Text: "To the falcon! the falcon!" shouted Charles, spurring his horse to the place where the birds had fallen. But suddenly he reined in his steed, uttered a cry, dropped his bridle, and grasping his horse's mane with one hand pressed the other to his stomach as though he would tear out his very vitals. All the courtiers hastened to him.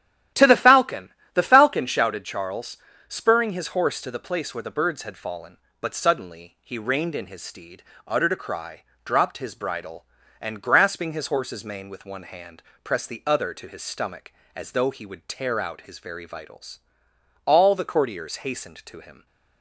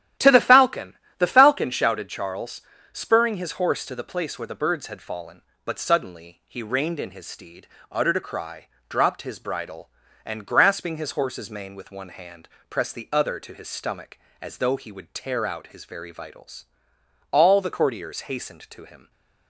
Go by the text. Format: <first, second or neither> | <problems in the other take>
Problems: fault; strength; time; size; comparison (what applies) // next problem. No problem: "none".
neither | starts louder than the rest; strong; the same in both // pauses between "hand" and "pressed"; slight; the same in both